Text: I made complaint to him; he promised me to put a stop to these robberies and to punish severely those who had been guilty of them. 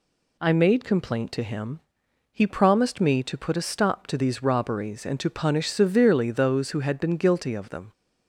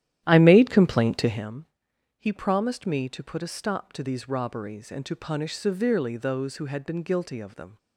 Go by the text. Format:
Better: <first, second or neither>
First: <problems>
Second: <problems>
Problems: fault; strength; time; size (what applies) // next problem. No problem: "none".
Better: first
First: none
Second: starts louder than the rest; strong; until 1.5 s; 12 dB